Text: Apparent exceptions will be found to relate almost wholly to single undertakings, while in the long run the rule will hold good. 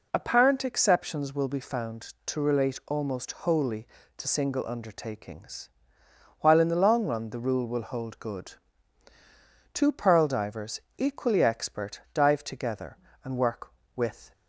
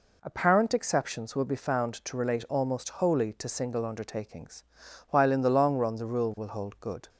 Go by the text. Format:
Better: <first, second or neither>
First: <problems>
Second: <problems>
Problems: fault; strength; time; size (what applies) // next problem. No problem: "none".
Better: second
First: goes on to say "Two pearl divers equally expert dive together and work with"; strong; from 9.7 s on; 4.5 s long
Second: none